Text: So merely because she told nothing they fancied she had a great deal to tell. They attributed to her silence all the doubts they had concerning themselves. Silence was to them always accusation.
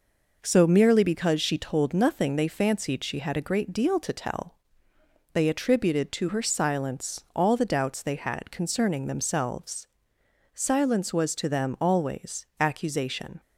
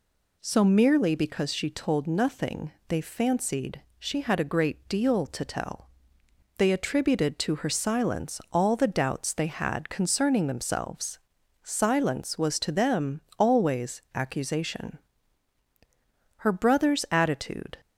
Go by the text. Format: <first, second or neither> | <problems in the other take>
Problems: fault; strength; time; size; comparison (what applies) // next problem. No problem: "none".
first | pauses between "nothing" and "they"; slight; at 2.7 s; 0.16 s long // pauses between "fancied" and "she"; slight; at 3.8 s; 0.16 s long // pauses between "them" and "always"; slight; at 13.2 s; 0.18 s long // goes on to say "Her brother's attitude"; from 16.3 s on; 1.4 s long